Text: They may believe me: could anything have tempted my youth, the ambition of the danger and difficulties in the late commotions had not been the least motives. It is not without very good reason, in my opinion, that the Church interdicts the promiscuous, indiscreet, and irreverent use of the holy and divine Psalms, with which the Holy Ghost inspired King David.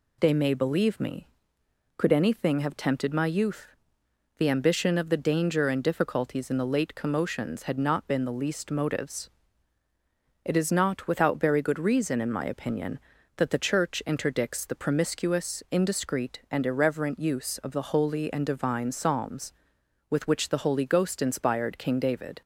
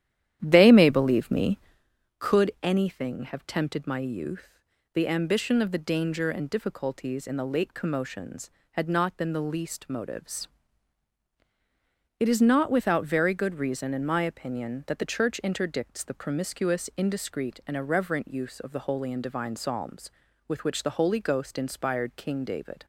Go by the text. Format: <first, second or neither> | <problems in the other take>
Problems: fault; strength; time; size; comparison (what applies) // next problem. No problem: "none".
first | starts louder than the rest; strong; until 1.9 s; 11 dB